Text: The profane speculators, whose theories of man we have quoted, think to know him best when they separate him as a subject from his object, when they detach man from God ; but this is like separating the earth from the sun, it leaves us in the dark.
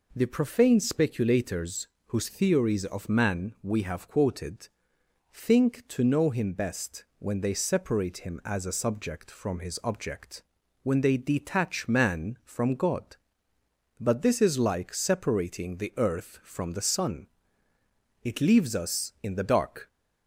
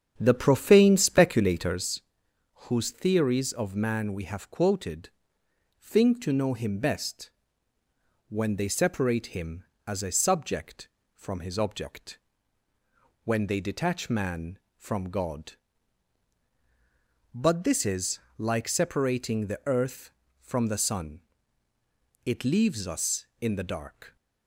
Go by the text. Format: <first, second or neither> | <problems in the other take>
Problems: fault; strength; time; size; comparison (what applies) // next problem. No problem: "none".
first | starts louder than the rest; strong; until 1.9 s; 8 dB // pauses between "best" and "when"; at 7.2 s; 1.0 s long // pauses between "is" and "like"; slight; at 18.1 s; 0.20 s long